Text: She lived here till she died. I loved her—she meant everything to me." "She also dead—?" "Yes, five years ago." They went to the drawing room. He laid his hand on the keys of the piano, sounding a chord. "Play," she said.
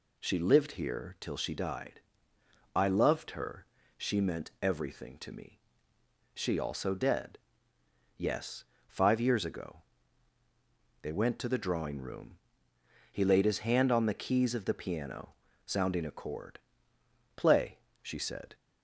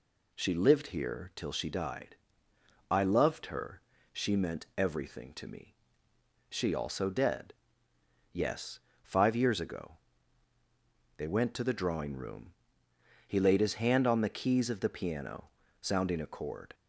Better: first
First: none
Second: stops before "Play she said"; at 16.7 s

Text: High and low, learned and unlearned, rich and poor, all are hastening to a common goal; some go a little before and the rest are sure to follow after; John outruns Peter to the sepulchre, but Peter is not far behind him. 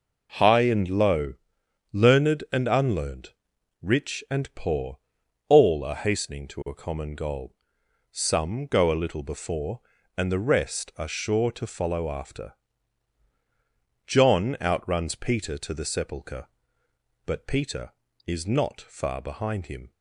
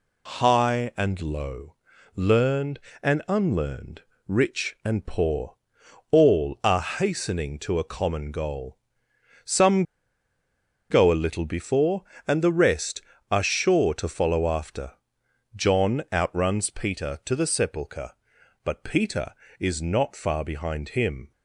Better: first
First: none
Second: pauses between "some" and "go"; at 9.8 s; 1.0 s long

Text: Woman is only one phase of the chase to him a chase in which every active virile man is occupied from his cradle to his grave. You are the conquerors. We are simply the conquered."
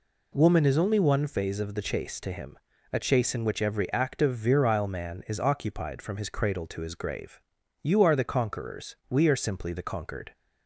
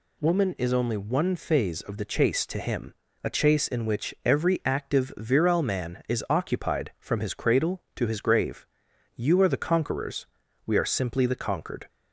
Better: neither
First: pauses between "him" and "a"; slight; at 2.5 s; 0.34 s long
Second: pauses between "him" and "a"; slight; at 2.9 s; 0.30 s long

